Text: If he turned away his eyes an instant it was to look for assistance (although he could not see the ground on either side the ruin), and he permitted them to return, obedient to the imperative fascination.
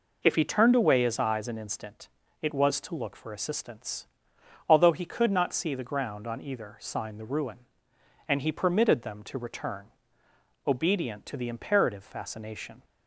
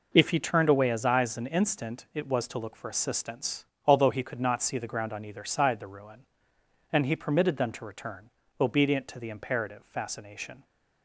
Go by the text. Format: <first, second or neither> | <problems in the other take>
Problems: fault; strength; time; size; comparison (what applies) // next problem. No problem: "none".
second | pauses between "instant" and "it"; slight; at 2.0 s; 0.34 s long // says "sign" for "side"; at 6.7 s